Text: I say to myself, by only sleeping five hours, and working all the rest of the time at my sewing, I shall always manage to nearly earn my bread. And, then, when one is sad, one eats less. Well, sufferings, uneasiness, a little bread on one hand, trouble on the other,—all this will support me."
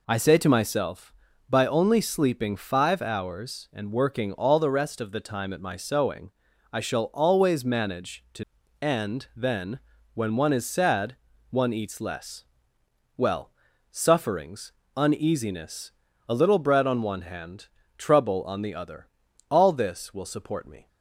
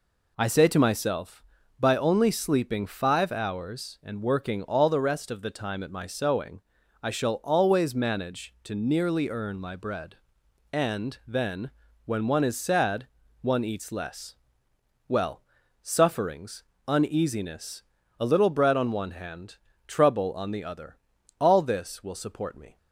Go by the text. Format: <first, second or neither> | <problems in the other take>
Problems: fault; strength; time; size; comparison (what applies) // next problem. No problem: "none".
second | skips "nearly earn my bread"; at 8.6 s